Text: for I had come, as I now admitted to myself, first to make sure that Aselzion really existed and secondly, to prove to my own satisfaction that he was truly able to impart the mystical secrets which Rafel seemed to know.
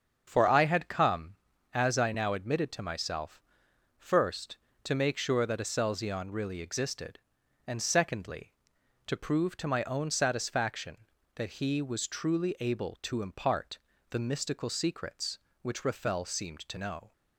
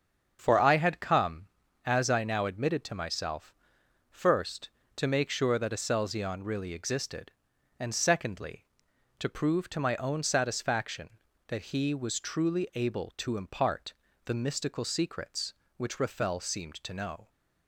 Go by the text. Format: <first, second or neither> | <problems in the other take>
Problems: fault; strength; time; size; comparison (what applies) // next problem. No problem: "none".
neither | starts louder than the rest; strong; the same in both // pauses between "impart" and "the"; slight; the same in both